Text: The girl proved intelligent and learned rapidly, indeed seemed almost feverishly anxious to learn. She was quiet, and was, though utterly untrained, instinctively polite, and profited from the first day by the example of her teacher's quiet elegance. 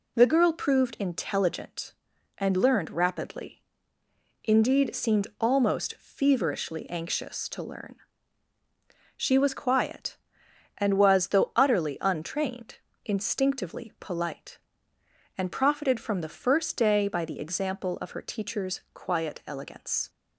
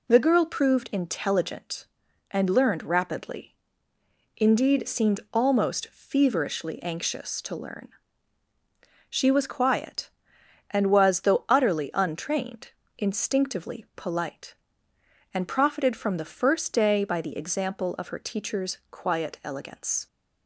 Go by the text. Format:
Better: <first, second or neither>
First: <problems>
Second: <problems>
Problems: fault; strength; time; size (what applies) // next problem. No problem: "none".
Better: neither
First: none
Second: none